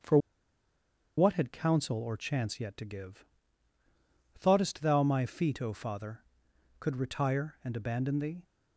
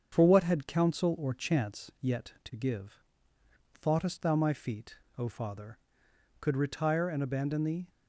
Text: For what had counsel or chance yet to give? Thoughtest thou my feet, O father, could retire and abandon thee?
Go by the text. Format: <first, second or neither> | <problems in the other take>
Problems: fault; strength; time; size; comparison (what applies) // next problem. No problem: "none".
second | starts louder than the rest; strong; until 2.0 s; 7.5 dB; strong in the second // pauses between "For" and "what"; at 0.1 s; 0.99 s long